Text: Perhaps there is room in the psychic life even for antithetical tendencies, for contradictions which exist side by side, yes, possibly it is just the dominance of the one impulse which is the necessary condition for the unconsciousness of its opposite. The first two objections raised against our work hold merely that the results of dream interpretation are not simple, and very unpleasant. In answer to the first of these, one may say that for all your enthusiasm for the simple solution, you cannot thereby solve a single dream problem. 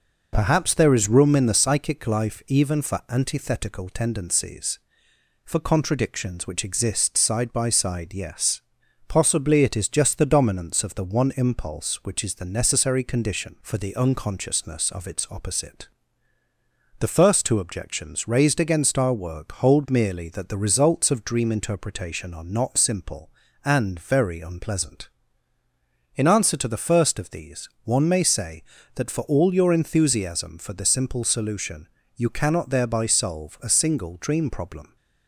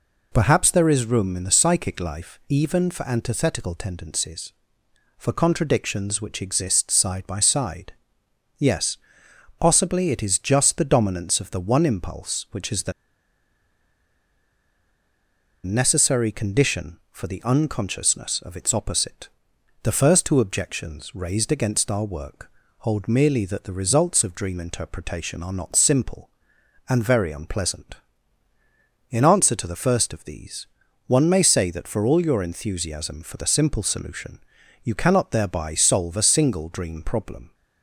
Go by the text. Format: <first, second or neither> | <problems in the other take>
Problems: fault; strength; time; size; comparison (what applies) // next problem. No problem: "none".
first | pauses between "the" and "necessary"; strong; at 12.9 s; 2.7 s long // pauses between "work" and "hold"; slight; at 22.5 s; 0.28 s long